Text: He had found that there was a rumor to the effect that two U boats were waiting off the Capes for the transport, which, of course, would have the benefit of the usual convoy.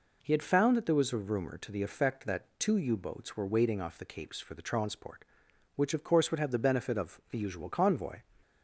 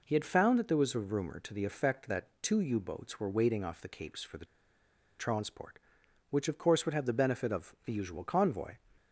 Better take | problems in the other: first | pauses between "the" and "transport"; noticeable; at 4.4 s; 0.73 s long

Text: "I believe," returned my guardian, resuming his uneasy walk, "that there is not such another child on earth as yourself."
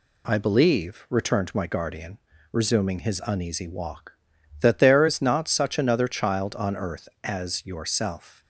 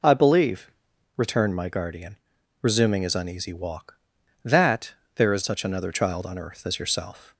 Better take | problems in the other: first | pauses between "that" and "there"; slight; at 4.9 s; 0.22 s long // skips "not"; at 5.4 s

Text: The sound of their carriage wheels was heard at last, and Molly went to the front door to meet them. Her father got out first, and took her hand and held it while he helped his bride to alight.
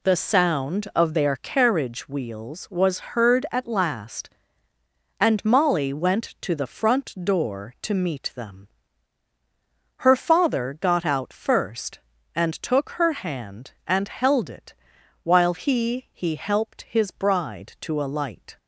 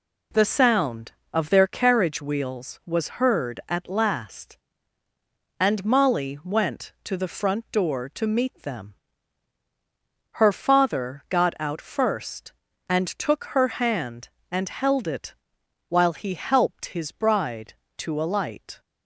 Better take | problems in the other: second | pauses between "it" and "while"; noticeable; at 14.7 s; 0.50 s long; noticeable in the second // says "he" twice; at 16.1 s

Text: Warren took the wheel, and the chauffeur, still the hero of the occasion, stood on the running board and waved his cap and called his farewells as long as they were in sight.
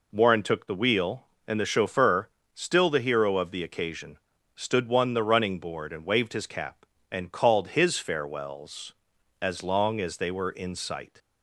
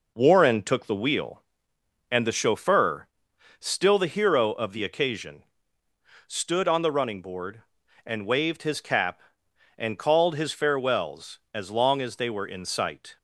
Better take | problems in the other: second | says "one" for "on"; at 4.8 s

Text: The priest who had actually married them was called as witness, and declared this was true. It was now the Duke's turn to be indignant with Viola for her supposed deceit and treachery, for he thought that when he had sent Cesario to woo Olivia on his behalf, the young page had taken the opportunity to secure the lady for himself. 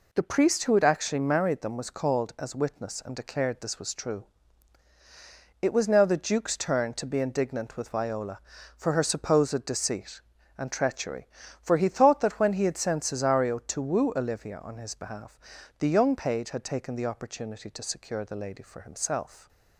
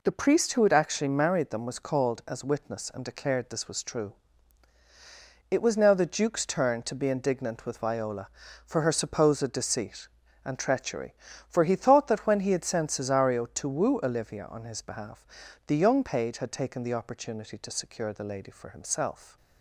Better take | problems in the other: neither | none

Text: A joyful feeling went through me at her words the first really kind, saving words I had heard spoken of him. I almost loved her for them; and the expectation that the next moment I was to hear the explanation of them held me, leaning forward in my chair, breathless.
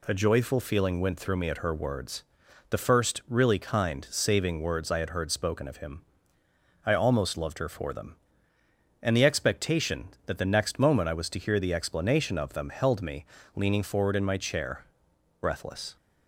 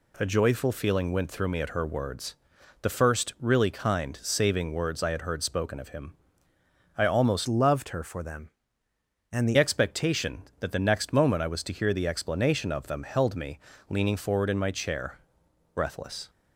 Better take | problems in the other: first | pauses between "words" and "the"; noticeable; at 2.3 s; 0.46 s long; noticeable in the first // changes voice from "loved" to "the"; from 7.4 to 9.5 s; 2.1 s long

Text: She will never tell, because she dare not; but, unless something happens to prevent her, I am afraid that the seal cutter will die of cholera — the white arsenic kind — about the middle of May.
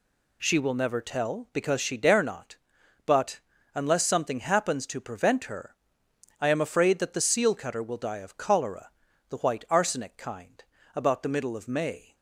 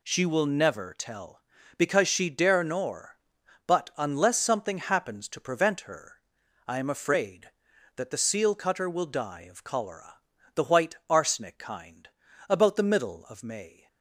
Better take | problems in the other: first | says "nor" for "not"; at 2.6 s

